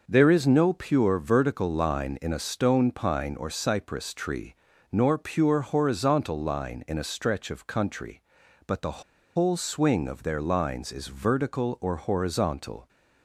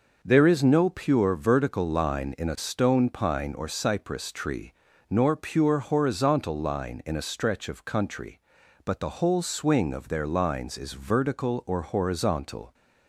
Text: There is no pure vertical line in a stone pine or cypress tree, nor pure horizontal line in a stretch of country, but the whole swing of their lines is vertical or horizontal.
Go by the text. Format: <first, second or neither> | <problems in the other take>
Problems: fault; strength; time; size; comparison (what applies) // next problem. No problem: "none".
second | pauses between "the" and "whole"; slight; at 9.0 s; 0.34 s long